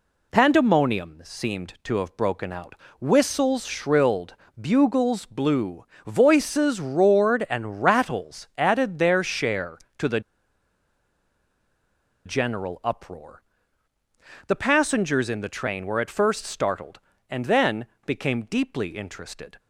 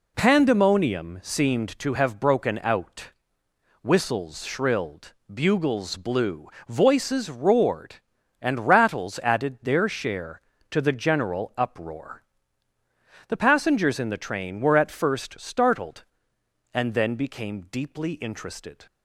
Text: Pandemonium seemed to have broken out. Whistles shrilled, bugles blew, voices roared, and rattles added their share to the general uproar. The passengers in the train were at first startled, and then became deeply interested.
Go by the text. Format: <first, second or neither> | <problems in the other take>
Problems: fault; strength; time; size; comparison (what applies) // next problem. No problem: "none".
second | pauses between "the" and "general"; strong; at 10.1 s; 2.0 s long // pauses between "then" and "became"; slight; at 17.8 s; 0.20 s long